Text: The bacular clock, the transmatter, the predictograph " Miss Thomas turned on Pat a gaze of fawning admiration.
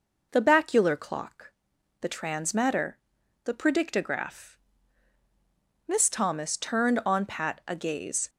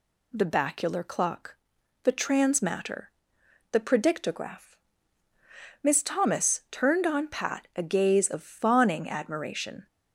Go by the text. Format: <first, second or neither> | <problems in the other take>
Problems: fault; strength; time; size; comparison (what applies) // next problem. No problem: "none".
second | starts louder than the rest; noticeable; until 1.3 s; 6 dB // stops before "of fawning admiration"; at 8.2 s